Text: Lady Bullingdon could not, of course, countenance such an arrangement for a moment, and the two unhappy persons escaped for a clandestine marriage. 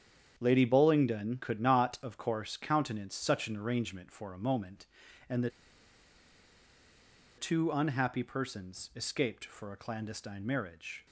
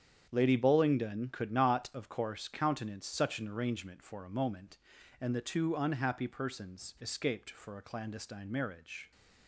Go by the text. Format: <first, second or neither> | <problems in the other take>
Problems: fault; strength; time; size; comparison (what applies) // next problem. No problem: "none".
second | starts louder than the rest; strong; until 1.3 s; 8.5 dB; strong in the second // pauses between "the" and "two"; strong; at 5.4 s; 1.8 s long